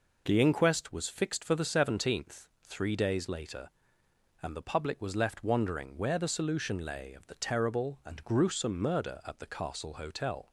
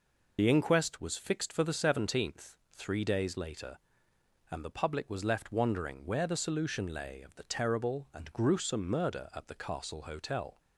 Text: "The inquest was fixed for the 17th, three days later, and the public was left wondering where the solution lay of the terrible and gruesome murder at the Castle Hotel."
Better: first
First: none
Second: loses the start of "The"; at 0.3 s; 45 ms

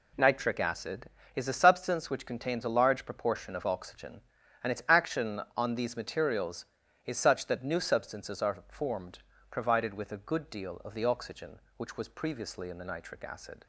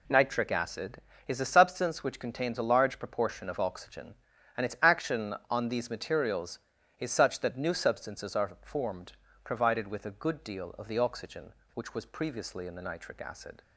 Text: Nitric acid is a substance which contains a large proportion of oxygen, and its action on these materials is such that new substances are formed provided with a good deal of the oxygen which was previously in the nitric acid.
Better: neither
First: pauses between "formed" and "provided"; slight; at 9.1 s; 0.30 s long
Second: pauses between "formed" and "provided"; slight; at 9.1 s; 0.30 s long

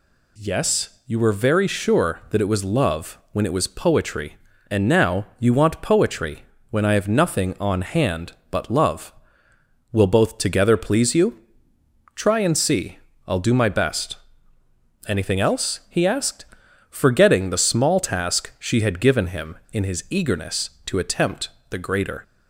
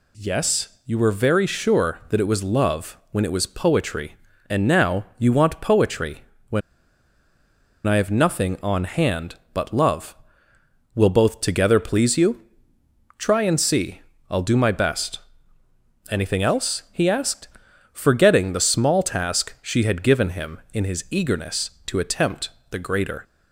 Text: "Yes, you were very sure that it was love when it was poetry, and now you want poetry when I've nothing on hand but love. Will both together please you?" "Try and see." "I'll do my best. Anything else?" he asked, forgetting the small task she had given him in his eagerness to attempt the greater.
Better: first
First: pauses between "poetry" and "when"; slight; at 6.4 s; 0.26 s long // pauses between "attempt" and "the"; slight; at 21.4 s; 0.20 s long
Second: pauses between "poetry" and "when"; slight; at 6.2 s; 0.26 s long // pauses between "when" and "I've"; strong; at 6.6 s; 1.2 s long // pauses between "attempt" and "the"; slight; at 22.4 s; 0.20 s long

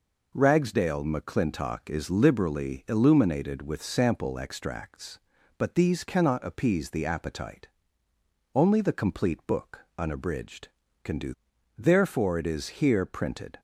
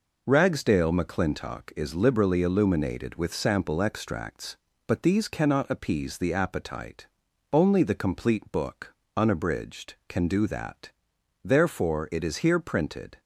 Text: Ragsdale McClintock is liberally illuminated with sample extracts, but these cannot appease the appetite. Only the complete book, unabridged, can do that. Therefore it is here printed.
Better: second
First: skips "that"; at 11.5 s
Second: none

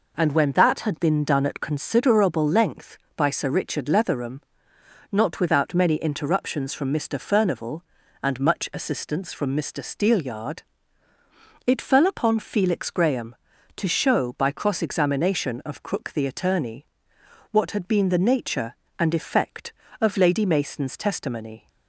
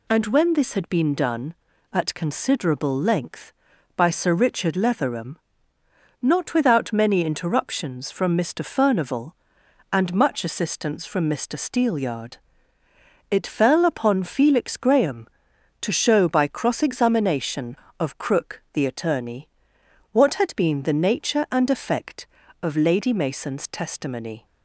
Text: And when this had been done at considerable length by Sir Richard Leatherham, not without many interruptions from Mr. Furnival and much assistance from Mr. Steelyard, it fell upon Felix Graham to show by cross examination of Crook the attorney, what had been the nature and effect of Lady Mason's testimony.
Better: second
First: says "that" for "this"; at 0.5 s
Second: none

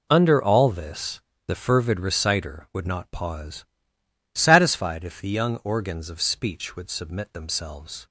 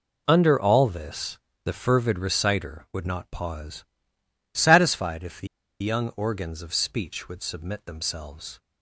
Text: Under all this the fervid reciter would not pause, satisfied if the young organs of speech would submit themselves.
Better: first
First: pauses between "this" and "the"; slight; at 1.1 s; 0.28 s long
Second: pauses between "this" and "the"; slight; at 1.3 s; 0.28 s long // pauses between "the" and "young"; slight; at 5.4 s; 0.35 s long

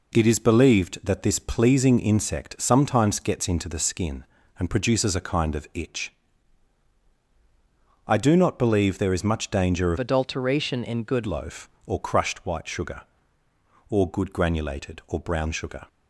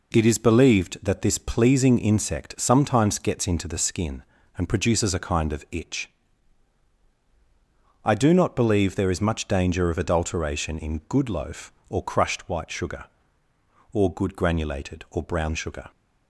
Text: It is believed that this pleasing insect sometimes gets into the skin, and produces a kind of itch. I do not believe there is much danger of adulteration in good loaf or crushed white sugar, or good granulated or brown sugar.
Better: second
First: changes voice from "adulteration" to "good"; from 9.9 to 11.2 s; 1.3 s long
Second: none

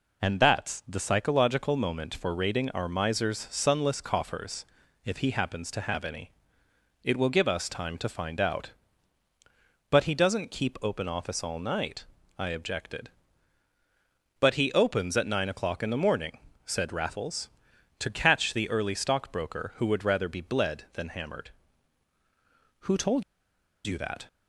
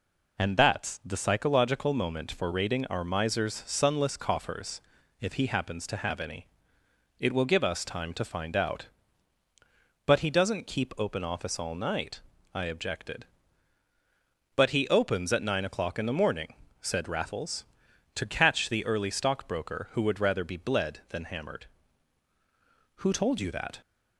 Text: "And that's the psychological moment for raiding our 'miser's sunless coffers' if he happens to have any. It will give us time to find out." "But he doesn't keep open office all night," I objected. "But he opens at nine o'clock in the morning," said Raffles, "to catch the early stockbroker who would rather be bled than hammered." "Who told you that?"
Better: second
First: pauses between "coffers" and "if"; at 4.6 s; 0.40 s long // pauses between "told" and "you"; noticeable; at 23.2 s; 0.63 s long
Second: pauses between "coffers" and "if"; at 4.7 s; 0.40 s long

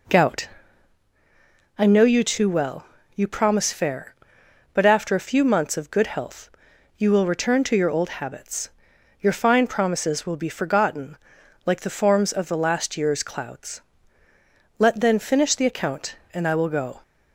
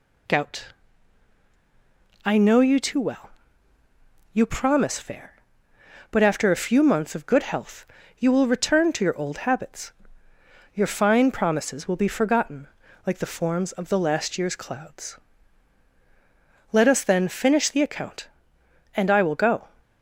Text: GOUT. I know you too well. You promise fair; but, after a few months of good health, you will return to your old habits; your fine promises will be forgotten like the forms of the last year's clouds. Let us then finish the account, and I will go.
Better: second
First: pauses between "forgotten" and "like"; noticeable; at 11.1 s; 0.48 s long // skips "us"; at 14.9 s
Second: pauses between "forgotten" and "like"; at 12.6 s; 0.38 s long

